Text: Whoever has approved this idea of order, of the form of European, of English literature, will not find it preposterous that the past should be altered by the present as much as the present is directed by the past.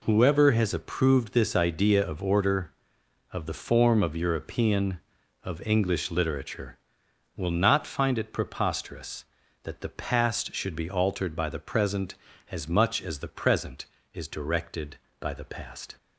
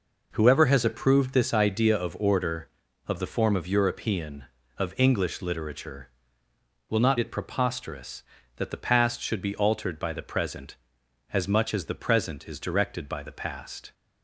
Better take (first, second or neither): first